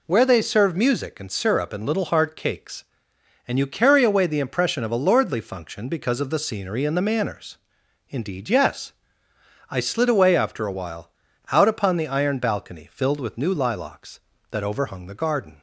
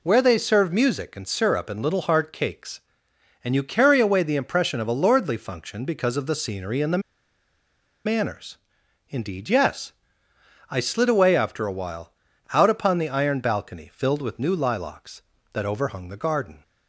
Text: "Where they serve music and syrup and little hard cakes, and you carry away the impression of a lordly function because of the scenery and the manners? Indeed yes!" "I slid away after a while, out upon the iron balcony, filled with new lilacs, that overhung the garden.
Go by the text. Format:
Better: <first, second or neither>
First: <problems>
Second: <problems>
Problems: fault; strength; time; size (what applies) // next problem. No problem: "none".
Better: first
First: none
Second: pauses between "the" and "manners"; at 7.0 s; 1.0 s long